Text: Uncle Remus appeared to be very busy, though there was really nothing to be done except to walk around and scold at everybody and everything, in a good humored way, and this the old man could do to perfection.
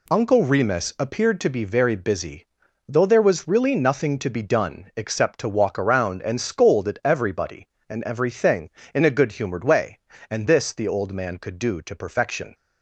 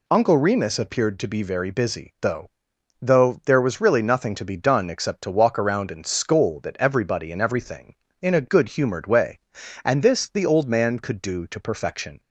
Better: first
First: none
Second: says "though" twice; at 3.0 s

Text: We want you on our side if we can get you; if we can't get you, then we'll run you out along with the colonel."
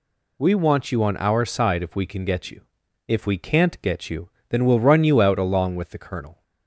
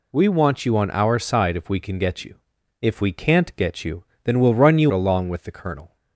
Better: first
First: none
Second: skips "out"; at 4.9 s

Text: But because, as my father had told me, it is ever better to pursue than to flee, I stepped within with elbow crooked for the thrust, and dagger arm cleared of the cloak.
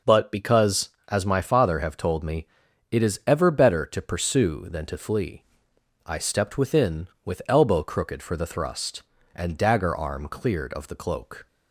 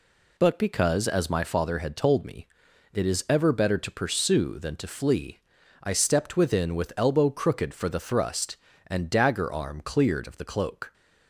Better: second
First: says "have" for "had"; at 1.7 s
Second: none

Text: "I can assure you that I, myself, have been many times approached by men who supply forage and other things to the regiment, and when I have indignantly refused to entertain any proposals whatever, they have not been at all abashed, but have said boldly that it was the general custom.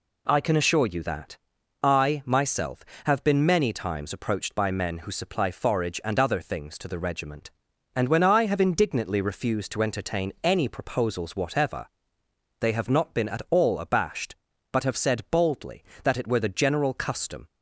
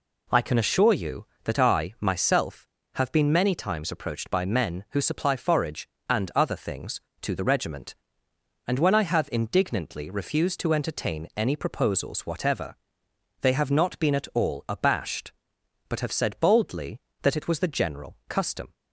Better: second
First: pauses between "that" and "I"; noticeable; at 1.3 s; 0.46 s long // says "were" for "was"; at 16.2 s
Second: none

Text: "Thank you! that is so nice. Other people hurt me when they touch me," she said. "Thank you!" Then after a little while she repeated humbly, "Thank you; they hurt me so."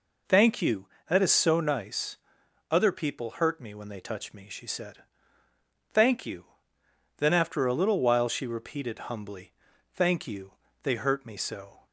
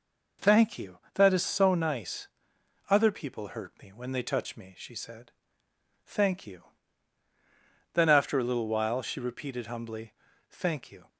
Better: first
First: none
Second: stops before "they hurt me so"; at 11.0 s

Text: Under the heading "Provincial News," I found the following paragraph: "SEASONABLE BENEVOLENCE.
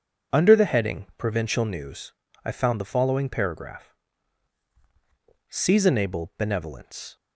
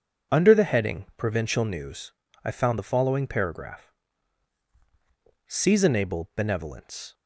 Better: neither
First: none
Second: none

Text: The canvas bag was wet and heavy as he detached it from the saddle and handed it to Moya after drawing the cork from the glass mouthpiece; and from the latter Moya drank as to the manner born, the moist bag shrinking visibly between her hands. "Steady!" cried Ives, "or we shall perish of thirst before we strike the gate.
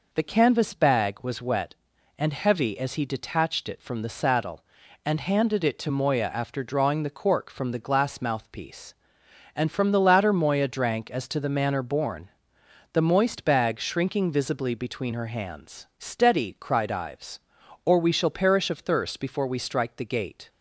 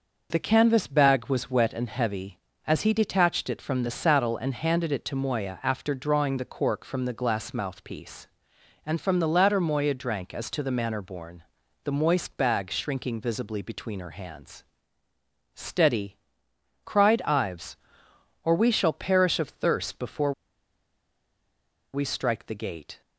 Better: first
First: none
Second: pauses between "before" and "we"; strong; at 20.3 s; 1.6 s long

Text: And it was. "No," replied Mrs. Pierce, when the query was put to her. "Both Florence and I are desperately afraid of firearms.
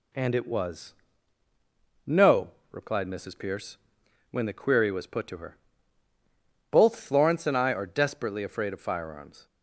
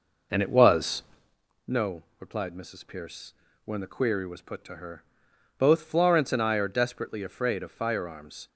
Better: first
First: none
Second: starts louder than the rest; noticeable; until 1.4 s; 5 dB

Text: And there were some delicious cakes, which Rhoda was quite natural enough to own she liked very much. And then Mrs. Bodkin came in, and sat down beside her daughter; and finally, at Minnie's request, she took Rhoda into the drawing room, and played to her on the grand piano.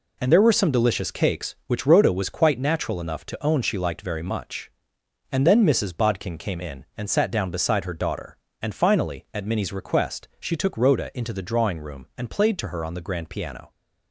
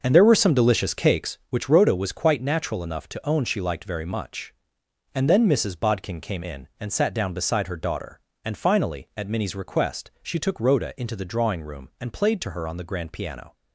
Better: first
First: none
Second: starts louder than the rest; noticeable; until 1.3 s; 6 dB

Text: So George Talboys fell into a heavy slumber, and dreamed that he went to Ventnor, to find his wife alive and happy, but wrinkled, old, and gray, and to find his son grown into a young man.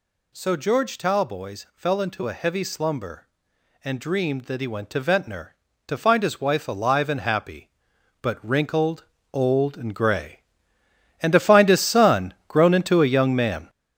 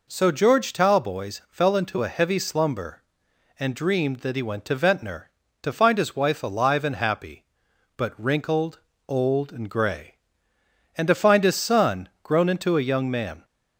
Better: second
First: gets louder; strong; throughout; 7.5 dB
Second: none

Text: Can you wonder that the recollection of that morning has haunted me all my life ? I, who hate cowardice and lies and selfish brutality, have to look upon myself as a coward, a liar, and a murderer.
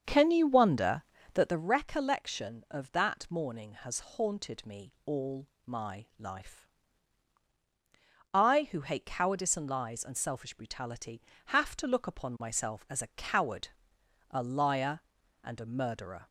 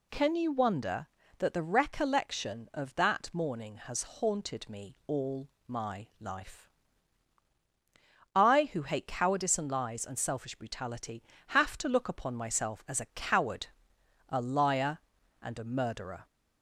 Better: second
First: starts louder than the rest; until 1.7 s; 7 dB // pauses between "all" and "my"; slight; at 5.4 s; 0.18 s long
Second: pauses between "all" and "my"; slight; at 5.4 s; 0.18 s long

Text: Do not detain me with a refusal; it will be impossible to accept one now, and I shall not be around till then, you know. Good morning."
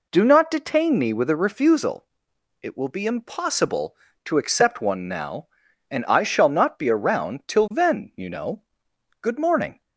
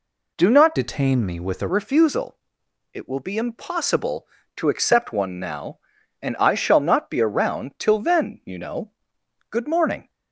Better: first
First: none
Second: changes voice from "detain" to "a"; from 0.7 to 1.6 s; 0.9 s long

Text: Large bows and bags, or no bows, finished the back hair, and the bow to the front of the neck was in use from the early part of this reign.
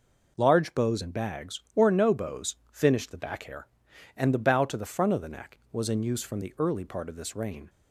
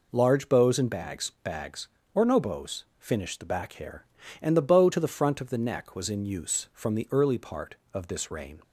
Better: first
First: none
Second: says "bags" twice; at 1.4 s

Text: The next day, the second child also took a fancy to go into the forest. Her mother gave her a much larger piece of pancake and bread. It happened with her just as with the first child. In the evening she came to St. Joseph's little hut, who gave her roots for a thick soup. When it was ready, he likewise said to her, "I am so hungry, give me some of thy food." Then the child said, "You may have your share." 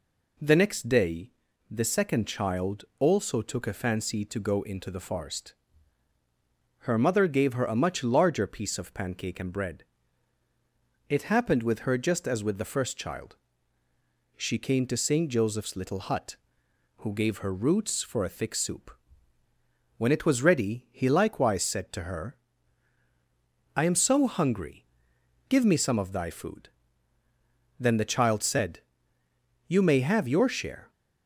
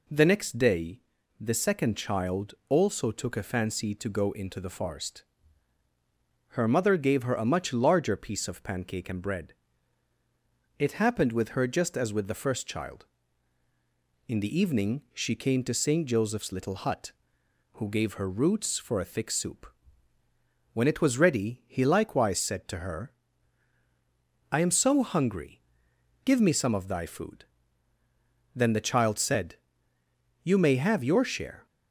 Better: second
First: skips "In the evening"; at 13.8 s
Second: none

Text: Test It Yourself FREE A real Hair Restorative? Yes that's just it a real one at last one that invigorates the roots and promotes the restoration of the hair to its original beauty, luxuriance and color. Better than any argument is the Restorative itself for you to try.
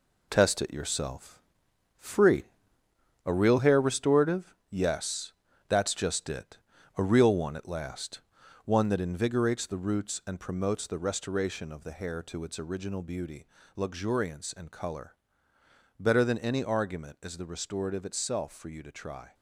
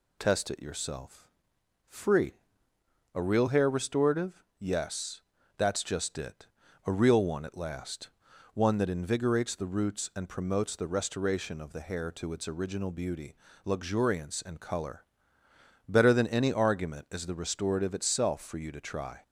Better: second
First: gets quieter; strong; throughout; 8 dB // pauses between "Yourself" and "FREE"; noticeable; at 1.4 s; 0.56 s long // pauses between "FREE" and "A"; noticeable; at 2.4 s; 0.82 s long // pauses between "Yes" and "that's"; slight; at 5.3 s; 0.36 s long // pauses between "it" and "a"; at 6.5 s; 0.40 s long // pauses between "last" and "one"; at 8.2 s; 0.44 s long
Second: pauses between "Yourself" and "FREE"; noticeable; at 1.3 s; 0.56 s long // pauses between "FREE" and "A"; noticeable; at 2.3 s; 0.82 s long // pauses between "Yes" and "that's"; slight; at 5.2 s; 0.36 s long // pauses between "it" and "a"; at 6.4 s; 0.40 s long // pauses between "last" and "one"; at 8.1 s; 0.44 s long

